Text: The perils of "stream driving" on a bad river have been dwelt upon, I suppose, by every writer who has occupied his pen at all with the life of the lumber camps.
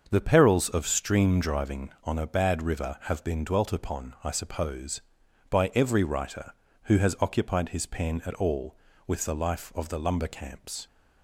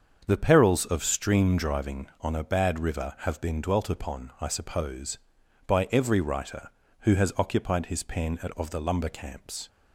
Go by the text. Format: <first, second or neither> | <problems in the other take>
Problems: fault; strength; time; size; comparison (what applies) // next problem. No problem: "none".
first | starts louder than the rest; until 1.2 s; 7 dB; also in the first // skips "all with the life"; at 8.5 s